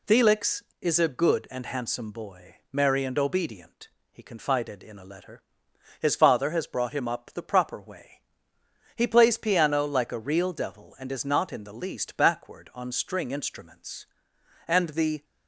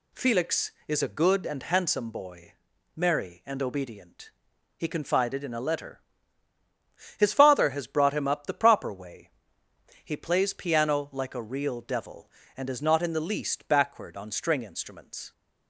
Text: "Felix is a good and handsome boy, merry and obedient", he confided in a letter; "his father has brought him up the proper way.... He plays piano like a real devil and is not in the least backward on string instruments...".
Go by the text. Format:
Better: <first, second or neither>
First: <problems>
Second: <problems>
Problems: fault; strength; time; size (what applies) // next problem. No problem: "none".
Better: second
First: goes on to say "And the"; from 14.6 s on; 0.56 s long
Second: none